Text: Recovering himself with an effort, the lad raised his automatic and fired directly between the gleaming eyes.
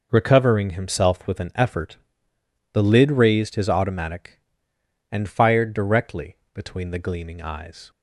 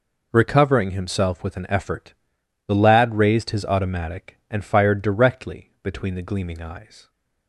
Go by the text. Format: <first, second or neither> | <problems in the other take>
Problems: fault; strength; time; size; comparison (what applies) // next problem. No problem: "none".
second | says "lid" for "lad"; at 2.8 s // pauses between "directly" and "between"; slight; at 6.3 s; 0.19 s long